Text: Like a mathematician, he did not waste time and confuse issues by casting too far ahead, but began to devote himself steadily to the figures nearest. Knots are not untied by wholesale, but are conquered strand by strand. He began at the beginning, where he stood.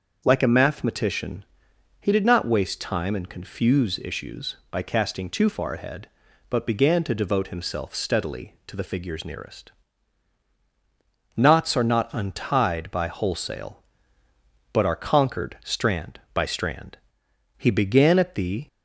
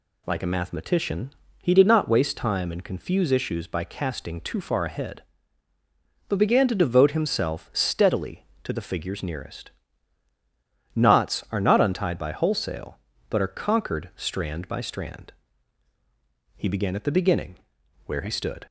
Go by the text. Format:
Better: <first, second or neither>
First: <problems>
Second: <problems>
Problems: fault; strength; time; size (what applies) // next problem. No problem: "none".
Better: second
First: starts louder than the rest; until 1.2 s; 6.5 dB // stops before "beginning where he stood"; at 18.6 s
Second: none